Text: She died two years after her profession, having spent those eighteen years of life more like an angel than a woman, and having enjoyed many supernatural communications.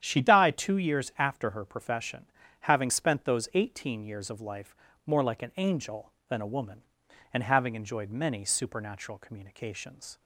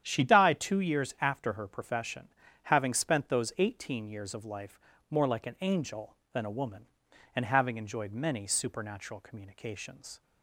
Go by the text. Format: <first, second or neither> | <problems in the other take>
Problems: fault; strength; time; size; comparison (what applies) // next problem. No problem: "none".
neither | starts louder than the rest; strong; the same in both // pauses between "life" and "more"; slight; the same in both